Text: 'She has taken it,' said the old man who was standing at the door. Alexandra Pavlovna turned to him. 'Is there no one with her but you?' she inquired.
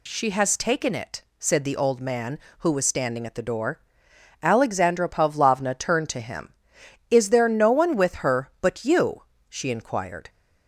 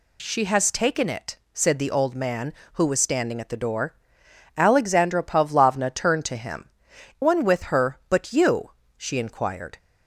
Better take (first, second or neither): first